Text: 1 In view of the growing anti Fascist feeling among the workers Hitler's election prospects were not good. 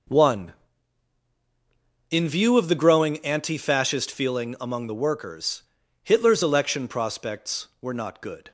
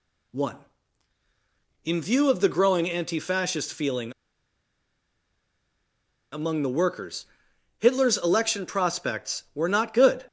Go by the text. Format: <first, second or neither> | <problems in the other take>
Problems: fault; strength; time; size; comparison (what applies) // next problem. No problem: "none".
first | pauses between "feeling" and "among"; strong; at 4.1 s; 2.2 s long // pauses between "workers" and "Hitler's"; noticeable; at 7.2 s; 0.52 s long; also in the first